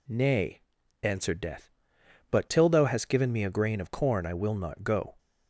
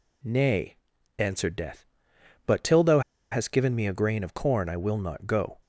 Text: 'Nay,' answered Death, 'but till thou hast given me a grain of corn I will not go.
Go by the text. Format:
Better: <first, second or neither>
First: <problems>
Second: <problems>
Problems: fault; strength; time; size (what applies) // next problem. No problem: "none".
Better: first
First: none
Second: pauses between "thou" and "hast"; slight; at 3.0 s; 0.30 s long